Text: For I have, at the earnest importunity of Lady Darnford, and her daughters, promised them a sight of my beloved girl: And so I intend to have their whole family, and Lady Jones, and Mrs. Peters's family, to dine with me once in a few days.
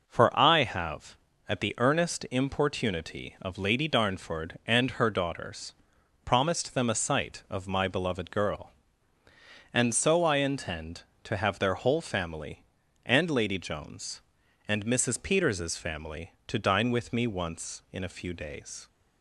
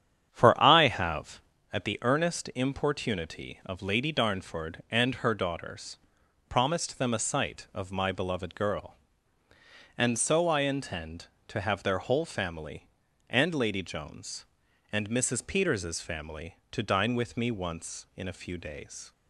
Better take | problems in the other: first | starts louder than the rest; strong; until 1.7 s; 9 dB

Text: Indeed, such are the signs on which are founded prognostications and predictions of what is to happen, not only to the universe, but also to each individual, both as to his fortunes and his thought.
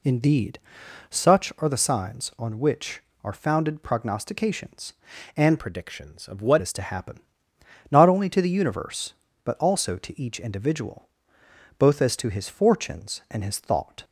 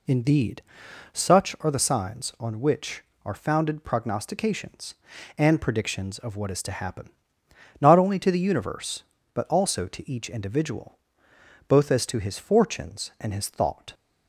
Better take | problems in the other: second | changes voice from "predictions" to "what"; from 5.5 to 6.5 s; 1.0 s long

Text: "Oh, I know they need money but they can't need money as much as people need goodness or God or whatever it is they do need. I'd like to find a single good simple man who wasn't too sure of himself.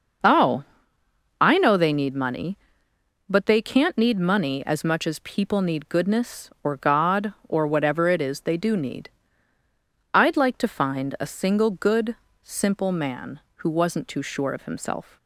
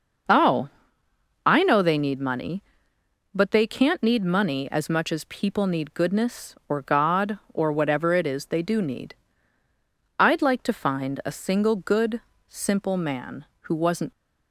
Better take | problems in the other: first | starts louder than the rest; noticeable; until 2.0 s; 6 dB; noticeable in the first // pauses between "good" and "simple"; slight; at 12.2 s; 0.26 s long; slight in the first // stops before "too sure of himself"; at 14.1 s

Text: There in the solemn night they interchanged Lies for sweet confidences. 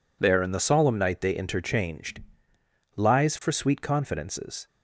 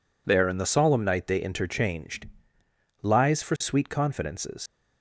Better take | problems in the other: first | pauses between "interchanged" and "Lies"; noticeable; at 2.2 s; 0.76 s long; noticeable in the first // leaves "confidences" unfinished; at 4.6 s; 85 ms

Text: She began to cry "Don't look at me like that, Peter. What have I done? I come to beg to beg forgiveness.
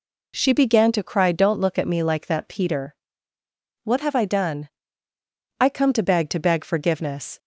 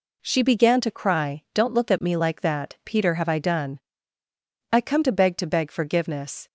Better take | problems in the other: first | skips "What"; at 3.1 s

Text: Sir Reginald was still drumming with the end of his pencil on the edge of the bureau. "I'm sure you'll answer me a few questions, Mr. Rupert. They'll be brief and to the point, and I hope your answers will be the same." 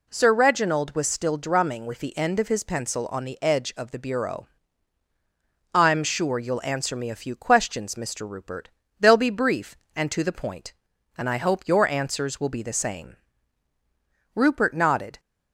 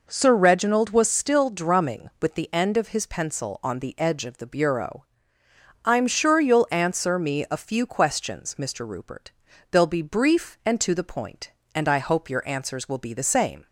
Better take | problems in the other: second | goes on to say "Rupert nodded"; noticeable; from 14.3 s on; 0.86 s long

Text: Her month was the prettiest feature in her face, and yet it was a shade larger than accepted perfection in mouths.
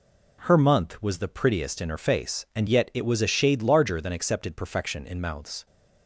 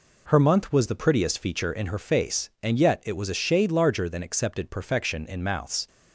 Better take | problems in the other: second | skips "feature"; at 1.8 s

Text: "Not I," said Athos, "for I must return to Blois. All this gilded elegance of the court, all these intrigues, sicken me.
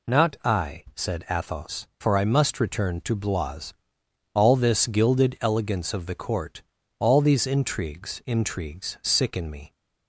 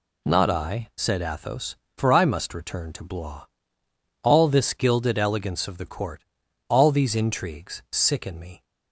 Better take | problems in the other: second | says "intrigues" twice; at 8.2 s

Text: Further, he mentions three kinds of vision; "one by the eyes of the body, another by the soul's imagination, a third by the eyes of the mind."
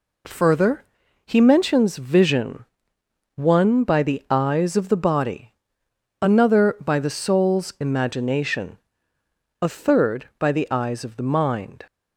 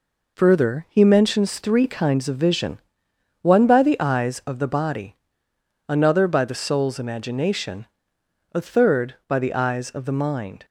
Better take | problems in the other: second | skips "three kinds of"; at 1.9 s

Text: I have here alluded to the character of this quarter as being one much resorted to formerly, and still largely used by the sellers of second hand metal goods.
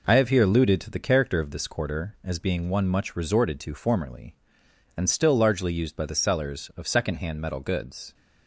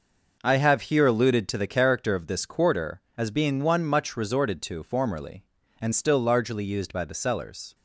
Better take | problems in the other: first | stops before "of second hand metal goods"; at 7.7 s

